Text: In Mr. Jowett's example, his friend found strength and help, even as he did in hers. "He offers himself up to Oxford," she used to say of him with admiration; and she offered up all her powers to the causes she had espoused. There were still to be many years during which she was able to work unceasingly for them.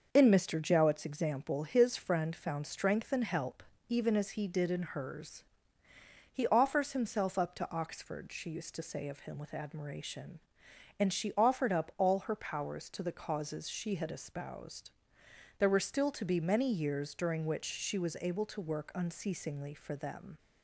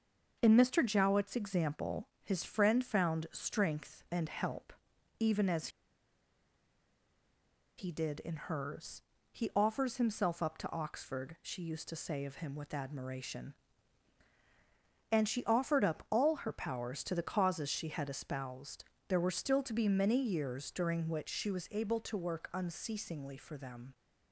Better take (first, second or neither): first